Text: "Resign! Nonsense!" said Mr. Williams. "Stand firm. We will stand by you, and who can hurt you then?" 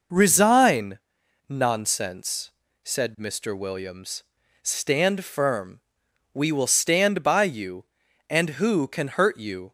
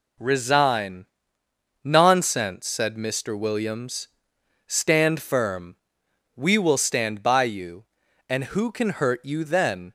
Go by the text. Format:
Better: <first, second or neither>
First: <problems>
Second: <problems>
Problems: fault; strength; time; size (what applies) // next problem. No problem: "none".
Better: second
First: stops before "then"; at 9.6 s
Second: none